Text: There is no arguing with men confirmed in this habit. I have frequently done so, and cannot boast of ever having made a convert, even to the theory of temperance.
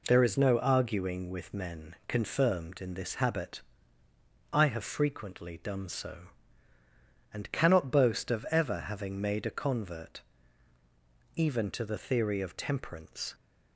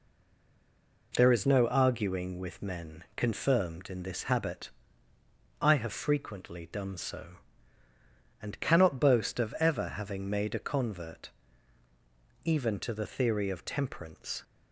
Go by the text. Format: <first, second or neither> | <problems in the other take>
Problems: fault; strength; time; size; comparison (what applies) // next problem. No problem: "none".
first | stays silent before the first word; until 1.1 s; 1.1 s long